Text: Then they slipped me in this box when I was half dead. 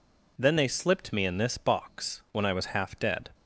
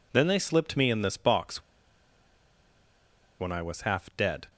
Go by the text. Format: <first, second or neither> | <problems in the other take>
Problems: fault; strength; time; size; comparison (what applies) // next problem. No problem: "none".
first | pauses between "box" and "when"; strong; at 1.6 s; 1.7 s long